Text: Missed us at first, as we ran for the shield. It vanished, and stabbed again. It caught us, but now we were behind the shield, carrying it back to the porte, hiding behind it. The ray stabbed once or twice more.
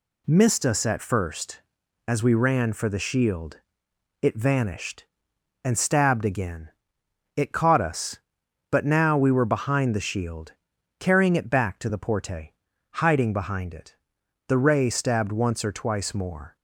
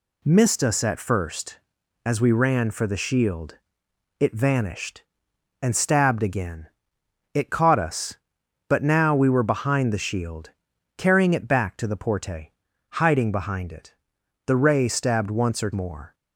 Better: first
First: none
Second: skips "twice"; at 15.7 s

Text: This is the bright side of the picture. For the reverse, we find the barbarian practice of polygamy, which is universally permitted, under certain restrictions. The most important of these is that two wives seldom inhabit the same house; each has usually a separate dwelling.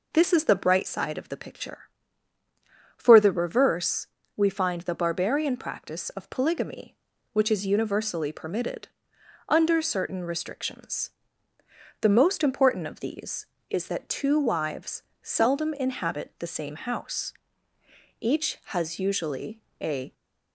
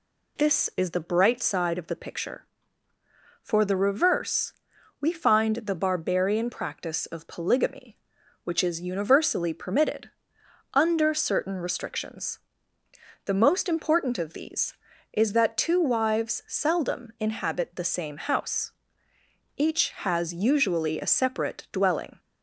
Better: second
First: pauses between "wives" and "seldom"; slight; at 15.0 s; 0.20 s long // pauses between "usually" and "a"; slight; at 19.6 s; 0.20 s long // stops before "separate dwelling"; at 20.1 s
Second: none

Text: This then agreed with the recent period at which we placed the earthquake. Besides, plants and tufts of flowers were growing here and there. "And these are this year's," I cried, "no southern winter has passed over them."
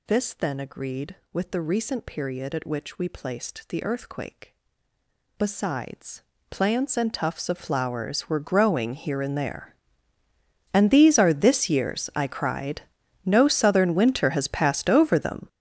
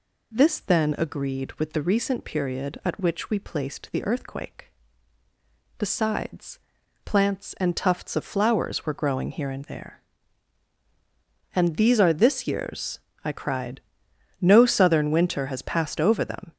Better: second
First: gets louder; strong; throughout; 13.5 dB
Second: none

